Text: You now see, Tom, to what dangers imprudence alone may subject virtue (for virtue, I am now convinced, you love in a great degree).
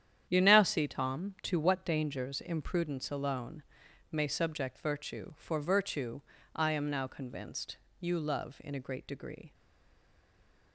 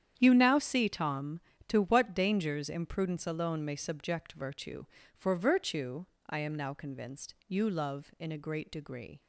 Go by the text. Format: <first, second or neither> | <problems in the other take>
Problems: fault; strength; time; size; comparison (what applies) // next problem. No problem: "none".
second | starts louder than the rest; strong; until 1.3 s; 9.5 dB; strong in the second // pauses between "alone" and "may"; noticeable; at 3.6 s; 0.50 s long // stays silent after the last word; noticeable; from 9.5 s on; 1.2 s long